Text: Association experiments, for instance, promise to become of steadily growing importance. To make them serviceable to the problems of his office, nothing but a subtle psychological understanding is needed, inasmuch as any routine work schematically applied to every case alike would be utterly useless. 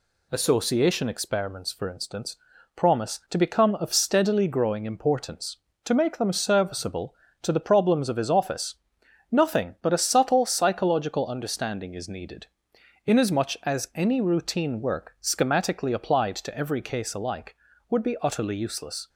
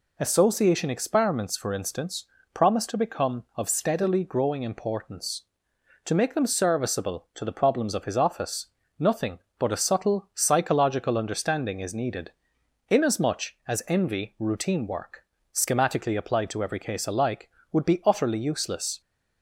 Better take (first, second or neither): first